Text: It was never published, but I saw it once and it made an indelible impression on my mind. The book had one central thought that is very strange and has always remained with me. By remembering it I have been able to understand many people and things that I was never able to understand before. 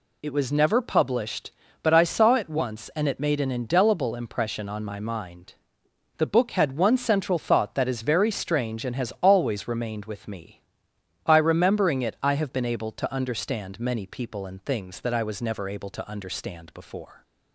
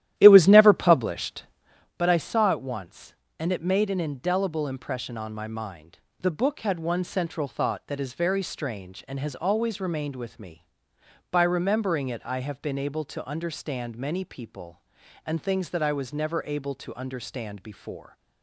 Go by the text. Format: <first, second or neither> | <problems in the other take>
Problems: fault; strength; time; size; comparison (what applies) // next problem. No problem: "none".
first | starts louder than the rest; strong; until 1.9 s; 13 dB